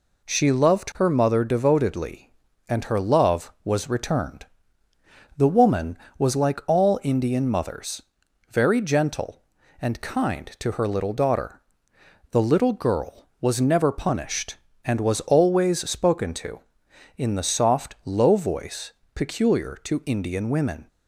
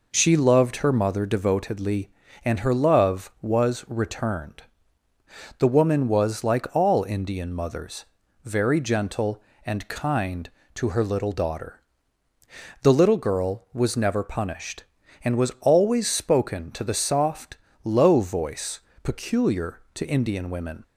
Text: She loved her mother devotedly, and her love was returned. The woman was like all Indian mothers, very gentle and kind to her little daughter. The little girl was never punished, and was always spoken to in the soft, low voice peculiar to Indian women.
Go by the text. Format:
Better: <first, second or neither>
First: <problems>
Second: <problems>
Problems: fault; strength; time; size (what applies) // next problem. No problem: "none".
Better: first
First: pauses between "voice" and "peculiar"; slight; at 18.9 s; 0.24 s long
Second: skips "in"; at 16.8 s // pauses between "voice" and "peculiar"; slight; at 18.8 s; 0.24 s long